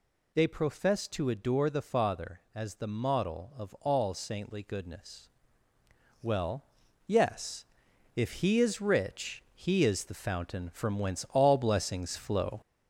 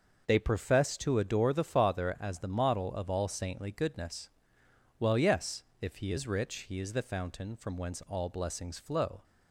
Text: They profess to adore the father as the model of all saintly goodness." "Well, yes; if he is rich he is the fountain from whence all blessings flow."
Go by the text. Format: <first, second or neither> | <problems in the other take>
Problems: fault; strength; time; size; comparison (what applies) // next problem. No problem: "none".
second | gets louder; throughout; 4 dB